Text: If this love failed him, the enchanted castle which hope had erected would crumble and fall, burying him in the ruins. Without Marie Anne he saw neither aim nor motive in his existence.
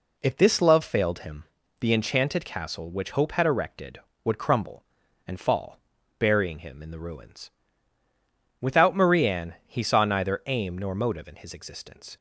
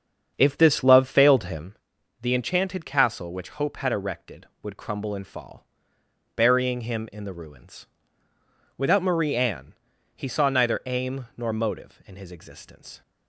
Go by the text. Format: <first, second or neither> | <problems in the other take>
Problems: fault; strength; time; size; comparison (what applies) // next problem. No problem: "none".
first | starts louder than the rest; strong; until 1.8 s; 7.5 dB // pauses between "Anne" and "he"; at 9.7 s; 0.42 s long